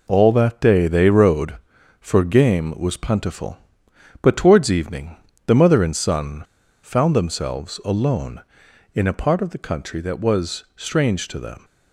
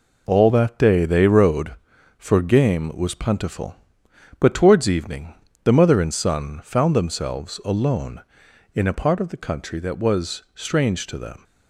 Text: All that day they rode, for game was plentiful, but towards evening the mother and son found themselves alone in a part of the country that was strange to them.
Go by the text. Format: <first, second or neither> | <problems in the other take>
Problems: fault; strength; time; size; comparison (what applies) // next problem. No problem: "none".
second | pauses between "evening" and "the"; slight; at 5.1 s; 0.30 s long; slight in the second // pauses between "son" and "found"; at 6.4 s; 0.40 s long